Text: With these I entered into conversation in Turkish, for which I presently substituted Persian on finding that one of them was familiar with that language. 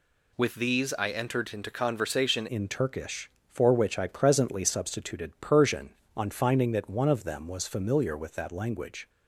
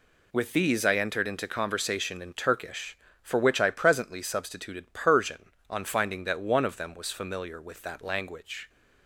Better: second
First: changes voice at "in"; from 2.4 s on; 6.6 s long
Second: none

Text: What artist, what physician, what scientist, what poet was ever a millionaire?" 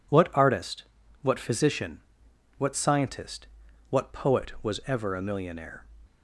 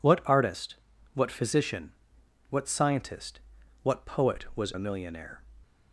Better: first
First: none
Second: skips "ever"; at 4.7 s

